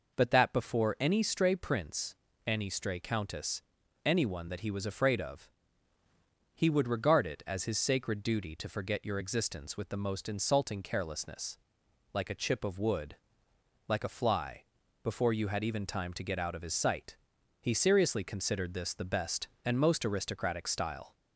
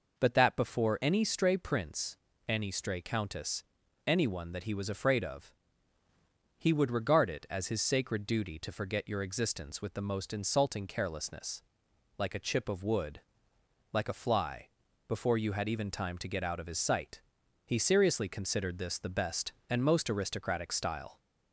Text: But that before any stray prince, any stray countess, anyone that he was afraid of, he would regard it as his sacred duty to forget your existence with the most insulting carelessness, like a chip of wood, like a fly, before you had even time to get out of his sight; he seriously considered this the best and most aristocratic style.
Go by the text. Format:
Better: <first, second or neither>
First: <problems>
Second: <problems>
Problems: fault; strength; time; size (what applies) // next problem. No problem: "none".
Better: neither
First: none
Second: none